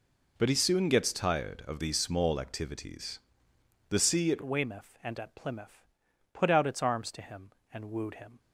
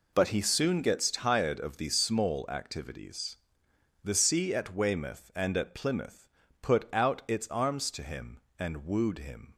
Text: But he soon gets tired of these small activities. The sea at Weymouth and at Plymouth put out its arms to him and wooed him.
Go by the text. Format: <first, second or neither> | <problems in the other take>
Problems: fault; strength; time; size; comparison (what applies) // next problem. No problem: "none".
second | changes voice at "Weymouth"; from 4.4 s on; 3.9 s long // pauses between "Plymouth" and "put"; noticeable; at 5.8 s; 0.48 s long; slight in the second